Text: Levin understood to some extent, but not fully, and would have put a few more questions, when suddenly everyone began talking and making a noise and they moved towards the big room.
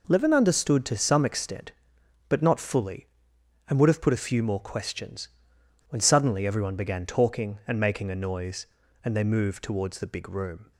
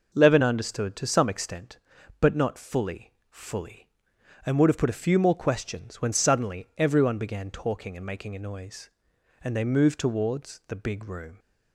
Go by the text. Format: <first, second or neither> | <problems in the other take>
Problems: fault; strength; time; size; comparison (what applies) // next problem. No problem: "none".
first | says "fully" twice; at 3.2 s